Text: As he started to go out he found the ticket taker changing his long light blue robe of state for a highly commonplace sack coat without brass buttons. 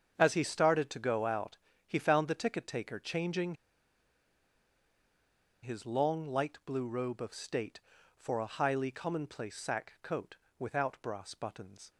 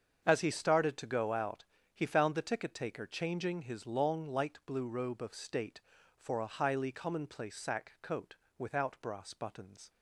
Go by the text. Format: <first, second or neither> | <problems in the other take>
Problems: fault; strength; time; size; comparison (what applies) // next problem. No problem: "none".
second | starts louder than the rest; strong; until 1.2 s; 7.5 dB; strong in the second // pauses between "out" and "he"; slight; at 1.5 s; 0.28 s long; slight in the second // pauses between "changing" and "his"; strong; at 3.5 s; 2.0 s long // pauses between "coat" and "without"; slight; at 10.3 s; 0.22 s long; slight in the second